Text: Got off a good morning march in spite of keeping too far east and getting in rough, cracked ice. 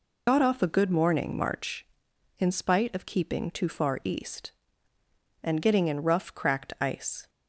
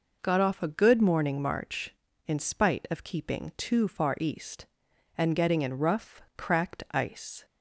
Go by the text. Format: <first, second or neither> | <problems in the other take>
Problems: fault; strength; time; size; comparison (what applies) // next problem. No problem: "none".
second | loses the start of "Got"; at 0.2 s; 65 ms